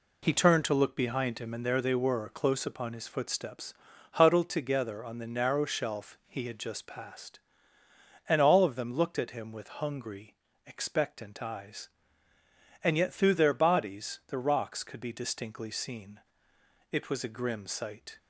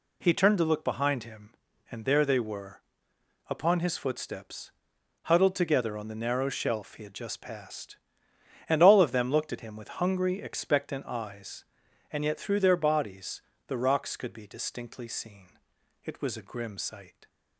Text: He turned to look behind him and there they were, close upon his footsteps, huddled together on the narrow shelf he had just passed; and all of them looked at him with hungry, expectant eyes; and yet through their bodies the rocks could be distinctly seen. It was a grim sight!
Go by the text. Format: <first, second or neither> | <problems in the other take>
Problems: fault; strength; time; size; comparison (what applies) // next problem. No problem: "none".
first | skips "close"; at 3.1 s // pauses between "bodies" and "the"; slight; at 13.3 s; 0.28 s long